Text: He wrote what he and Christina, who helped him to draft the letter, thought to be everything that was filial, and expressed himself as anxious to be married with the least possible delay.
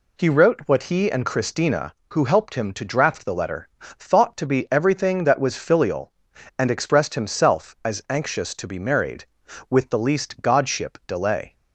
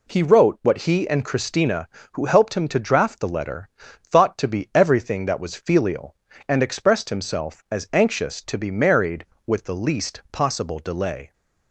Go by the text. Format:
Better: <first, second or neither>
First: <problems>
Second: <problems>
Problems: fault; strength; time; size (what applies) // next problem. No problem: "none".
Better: second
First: says "godship" for "possible"; at 10.4 s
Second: none